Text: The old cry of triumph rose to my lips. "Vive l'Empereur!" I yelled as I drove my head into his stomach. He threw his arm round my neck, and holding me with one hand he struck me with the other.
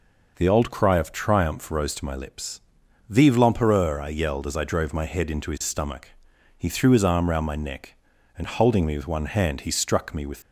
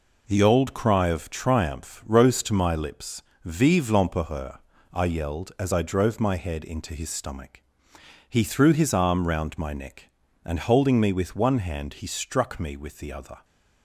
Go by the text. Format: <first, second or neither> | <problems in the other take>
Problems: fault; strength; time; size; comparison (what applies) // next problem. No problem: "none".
second | stops before "the other"; at 10.4 s